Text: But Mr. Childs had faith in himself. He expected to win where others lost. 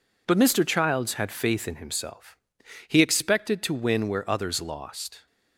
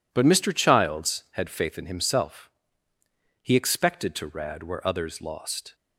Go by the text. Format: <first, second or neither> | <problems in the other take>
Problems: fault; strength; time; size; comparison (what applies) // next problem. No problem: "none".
first | says "rad" for "win"; at 4.2 s